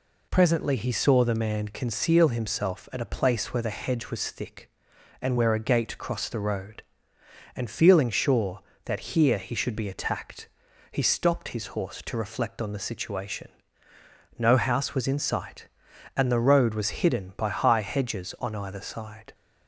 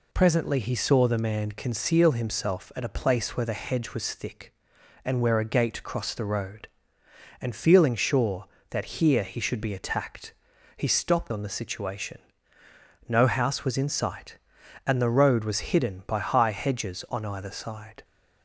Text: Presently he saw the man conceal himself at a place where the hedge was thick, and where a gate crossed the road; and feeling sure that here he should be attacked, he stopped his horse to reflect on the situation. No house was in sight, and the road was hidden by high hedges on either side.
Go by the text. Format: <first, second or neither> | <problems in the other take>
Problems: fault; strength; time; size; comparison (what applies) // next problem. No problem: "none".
first | skips "his horse to reflect"; at 11.3 s